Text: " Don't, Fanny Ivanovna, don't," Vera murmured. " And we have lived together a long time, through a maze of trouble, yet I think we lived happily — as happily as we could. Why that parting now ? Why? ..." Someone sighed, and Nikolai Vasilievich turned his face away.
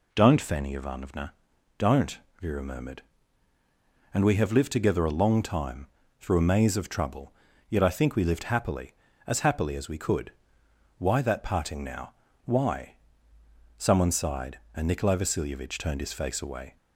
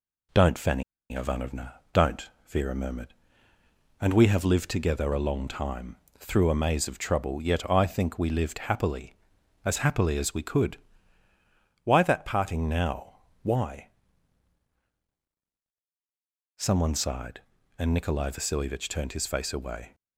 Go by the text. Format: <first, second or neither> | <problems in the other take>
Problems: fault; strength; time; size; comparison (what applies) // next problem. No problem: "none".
first | pauses between "Fanny" and "Ivanovna"; slight; at 0.8 s; 0.29 s long